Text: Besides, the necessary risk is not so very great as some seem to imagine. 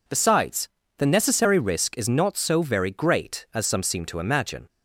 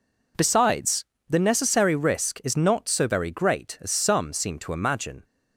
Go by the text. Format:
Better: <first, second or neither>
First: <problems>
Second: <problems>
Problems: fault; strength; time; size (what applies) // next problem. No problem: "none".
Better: neither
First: none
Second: none